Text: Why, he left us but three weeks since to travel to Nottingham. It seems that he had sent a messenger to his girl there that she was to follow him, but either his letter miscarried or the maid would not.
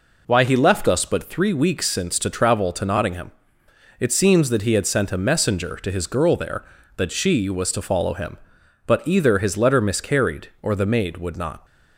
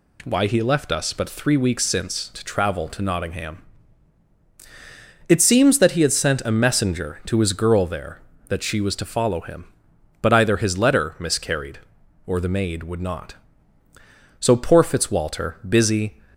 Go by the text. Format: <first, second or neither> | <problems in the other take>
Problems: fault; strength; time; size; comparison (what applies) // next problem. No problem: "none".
first | goes on to say "So poor Fitzwalter busy"; strong; from 14.3 s on; 1.8 s long